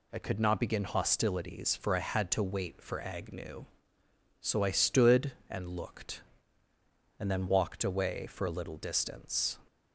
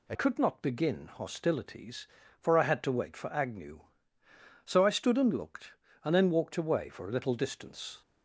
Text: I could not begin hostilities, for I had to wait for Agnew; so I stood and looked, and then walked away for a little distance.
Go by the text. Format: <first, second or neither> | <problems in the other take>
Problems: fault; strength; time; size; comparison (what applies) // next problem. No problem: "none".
first | changes voice at "could"; from 0.1 s on; 7.9 s long